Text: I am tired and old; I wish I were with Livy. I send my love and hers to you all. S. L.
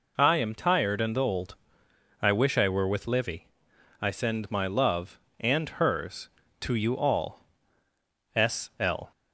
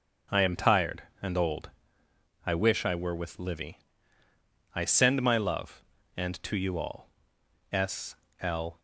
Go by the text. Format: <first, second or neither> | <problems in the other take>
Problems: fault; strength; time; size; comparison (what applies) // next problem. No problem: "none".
first | skips "hers"; at 6.4 s // pauses between "S" and "L"; slight; at 8.1 s; 0.24 s long